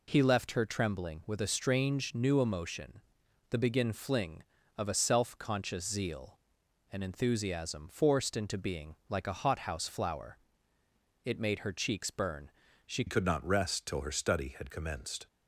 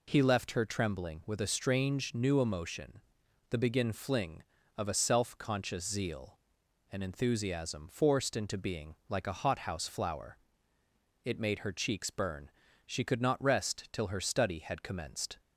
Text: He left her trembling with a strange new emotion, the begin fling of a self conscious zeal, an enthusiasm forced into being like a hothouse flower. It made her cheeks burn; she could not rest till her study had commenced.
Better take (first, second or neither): second